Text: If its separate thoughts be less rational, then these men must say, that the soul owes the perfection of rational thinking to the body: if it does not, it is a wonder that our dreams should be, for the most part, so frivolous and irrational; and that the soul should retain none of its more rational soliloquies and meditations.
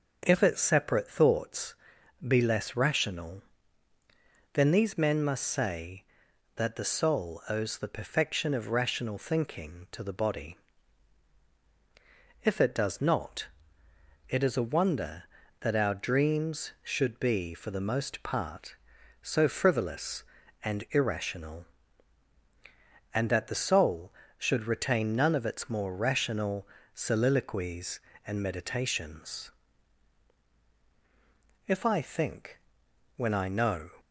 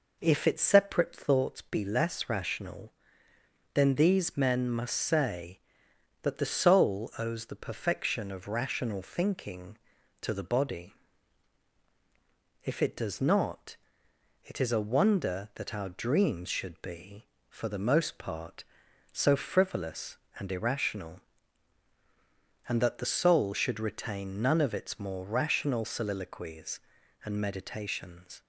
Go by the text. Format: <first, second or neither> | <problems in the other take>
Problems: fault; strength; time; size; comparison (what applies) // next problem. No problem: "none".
second | starts louder than the rest; until 1.2 s; 6.5 dB // pauses between "thoughts" and "be"; noticeable; at 1.7 s; 0.50 s long // pauses between "rational" and "soliloquies"; slight; at 26.6 s; 0.26 s long // goes on to say "If I think when I know"; strong; from 31.6 s on; 2.2 s long